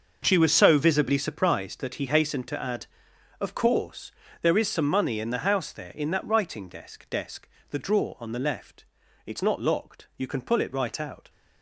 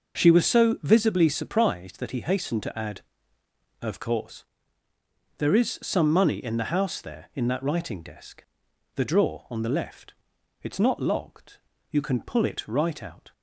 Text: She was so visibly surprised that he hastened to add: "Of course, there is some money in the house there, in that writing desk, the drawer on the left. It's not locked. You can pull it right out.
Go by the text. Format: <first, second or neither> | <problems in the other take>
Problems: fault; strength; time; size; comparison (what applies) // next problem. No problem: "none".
second | starts louder than the rest; noticeable; until 1.2 s; 6 dB // says "desk" twice; at 7.0 s